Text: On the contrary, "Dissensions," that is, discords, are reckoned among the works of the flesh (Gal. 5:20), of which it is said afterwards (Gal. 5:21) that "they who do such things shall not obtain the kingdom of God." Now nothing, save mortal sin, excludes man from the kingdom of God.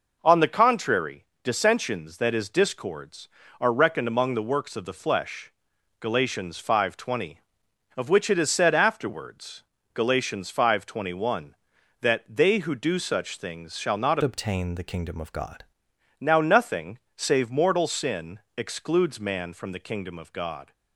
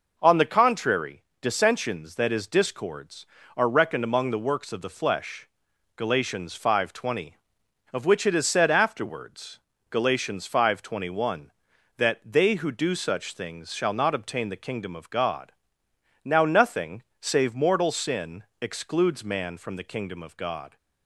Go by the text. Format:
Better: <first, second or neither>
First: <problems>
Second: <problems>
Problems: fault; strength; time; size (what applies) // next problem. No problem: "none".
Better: second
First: changes voice from "obtain" to "God"; from 14.2 to 15.6 s; 1.4 s long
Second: none